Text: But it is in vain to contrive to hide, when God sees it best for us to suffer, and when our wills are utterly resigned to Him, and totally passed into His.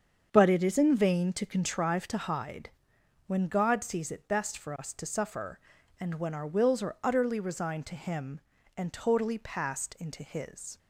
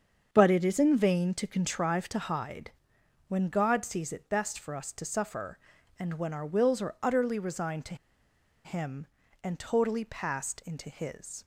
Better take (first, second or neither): first